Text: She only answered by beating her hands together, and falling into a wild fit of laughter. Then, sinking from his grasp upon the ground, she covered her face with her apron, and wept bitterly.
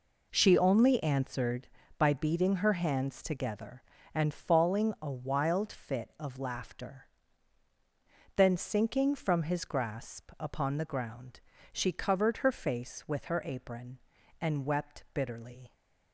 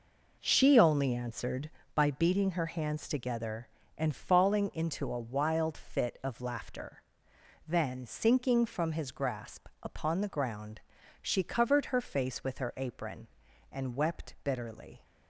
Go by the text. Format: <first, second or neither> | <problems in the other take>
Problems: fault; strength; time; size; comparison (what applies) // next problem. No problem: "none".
second | skips "into"; at 4.9 s